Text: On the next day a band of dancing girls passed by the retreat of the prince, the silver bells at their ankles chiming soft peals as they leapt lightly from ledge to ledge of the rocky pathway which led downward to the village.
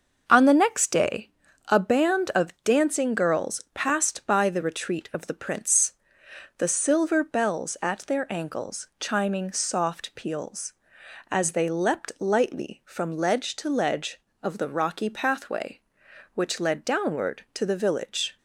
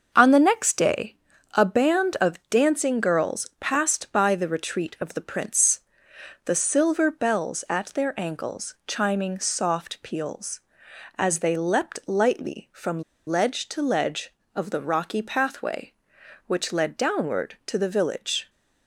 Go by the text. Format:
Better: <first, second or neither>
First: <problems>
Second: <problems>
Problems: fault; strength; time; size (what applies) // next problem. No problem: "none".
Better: first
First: starts louder than the rest; noticeable; until 1.2 s; 6 dB // pauses between "day" and "a"; at 1.3 s; 0.38 s long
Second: starts louder than the rest; until 1.1 s; 6 dB // pauses between "day" and "a"; at 1.1 s; 0.38 s long // pauses between "from" and "ledge"; slight; at 13.0 s; 0.26 s long